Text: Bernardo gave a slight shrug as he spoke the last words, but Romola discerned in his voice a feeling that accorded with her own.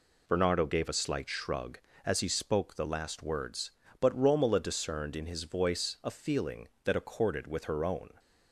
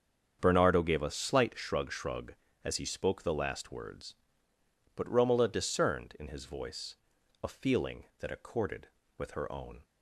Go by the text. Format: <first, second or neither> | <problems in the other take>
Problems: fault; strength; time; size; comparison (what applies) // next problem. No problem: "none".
first | starts louder than the rest; strong; until 1.4 s; 7.5 dB // says "shrug" twice; at 1.9 s // pauses between "voice" and "a"; noticeable; at 6.9 s; 0.46 s long